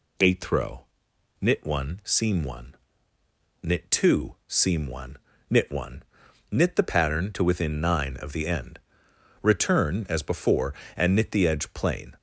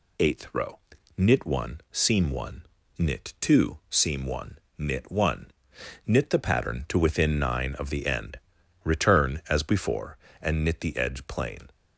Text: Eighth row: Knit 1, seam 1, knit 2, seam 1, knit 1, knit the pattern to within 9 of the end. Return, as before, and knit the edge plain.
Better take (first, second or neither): neither